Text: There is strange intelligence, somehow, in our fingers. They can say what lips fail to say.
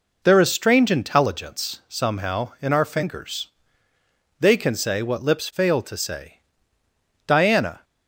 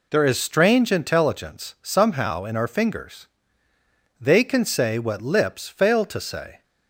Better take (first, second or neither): second